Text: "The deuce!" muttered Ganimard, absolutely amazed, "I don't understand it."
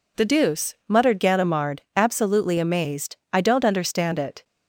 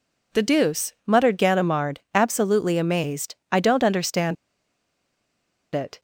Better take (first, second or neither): first